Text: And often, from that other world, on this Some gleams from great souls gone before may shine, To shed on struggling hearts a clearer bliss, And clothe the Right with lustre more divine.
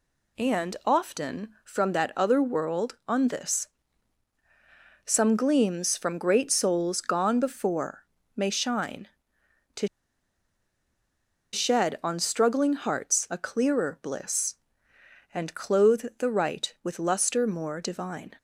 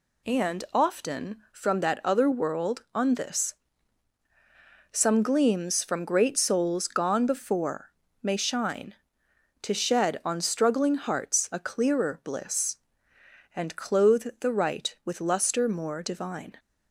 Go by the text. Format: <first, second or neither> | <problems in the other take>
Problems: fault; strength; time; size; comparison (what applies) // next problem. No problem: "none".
second | pauses between "this" and "Some"; strong; at 3.6 s; 1.3 s long; strong in the second // pauses between "before" and "may"; slight; at 8.0 s; 0.30 s long; slight in the second // pauses between "To" and "shed"; strong; at 9.8 s; 1.6 s long